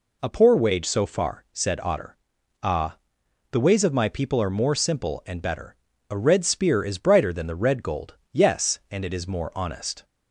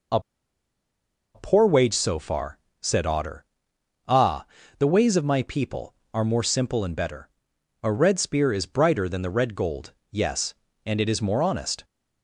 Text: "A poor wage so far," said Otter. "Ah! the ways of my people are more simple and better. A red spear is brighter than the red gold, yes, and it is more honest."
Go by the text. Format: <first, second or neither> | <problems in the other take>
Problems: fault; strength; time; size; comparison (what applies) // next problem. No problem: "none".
first | pauses between "A" and "poor"; at 0.1 s; 1.1 s long